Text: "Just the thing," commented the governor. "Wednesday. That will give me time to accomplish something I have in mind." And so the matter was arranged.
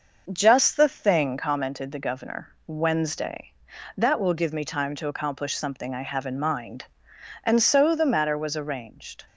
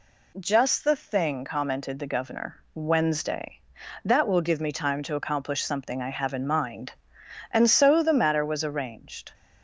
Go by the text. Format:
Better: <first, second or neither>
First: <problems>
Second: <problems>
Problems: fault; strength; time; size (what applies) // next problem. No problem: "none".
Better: second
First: starts louder than the rest; noticeable; until 1.7 s; 6 dB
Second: none